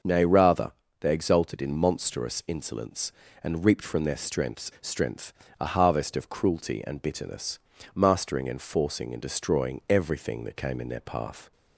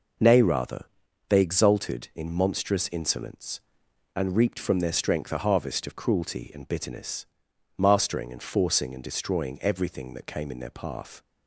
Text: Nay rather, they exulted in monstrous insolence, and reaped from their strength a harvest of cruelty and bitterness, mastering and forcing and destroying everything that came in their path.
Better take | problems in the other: second | starts louder than the rest; until 1.3 s; 6.5 dB // says "strength" twice; at 4.8 s

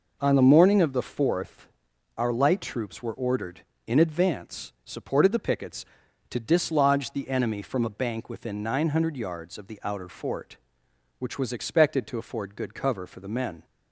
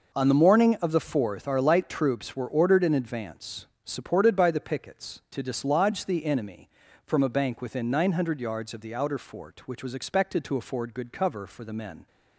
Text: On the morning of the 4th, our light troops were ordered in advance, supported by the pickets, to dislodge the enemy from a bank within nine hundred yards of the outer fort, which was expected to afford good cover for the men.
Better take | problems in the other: second | skips "by"; at 5.3 s

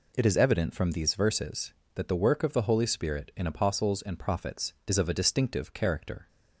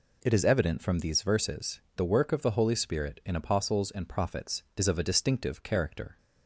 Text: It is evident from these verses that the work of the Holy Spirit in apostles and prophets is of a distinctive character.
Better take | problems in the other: first | skips "that"; at 1.8 s

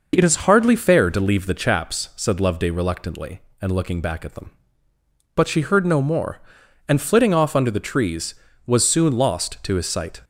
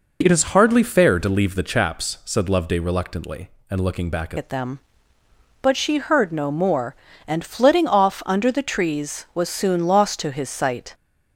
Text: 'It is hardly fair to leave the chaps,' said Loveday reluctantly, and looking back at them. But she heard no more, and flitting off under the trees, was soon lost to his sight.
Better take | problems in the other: first | changes voice at "at"; from 4.3 s on; 6.6 s long

